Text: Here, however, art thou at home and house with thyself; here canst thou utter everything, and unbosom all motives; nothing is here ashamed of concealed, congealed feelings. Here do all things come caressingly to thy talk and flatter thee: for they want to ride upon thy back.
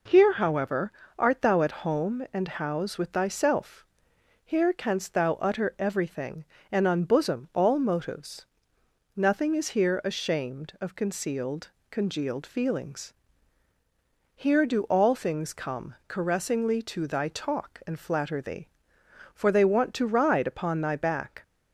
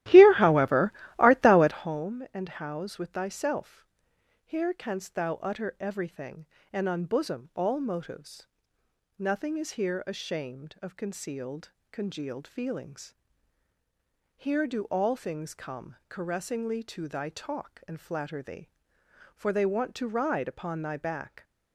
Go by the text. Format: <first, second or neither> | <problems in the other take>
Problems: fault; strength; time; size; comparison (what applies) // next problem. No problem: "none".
first | starts louder than the rest; strong; until 1.9 s; 14.5 dB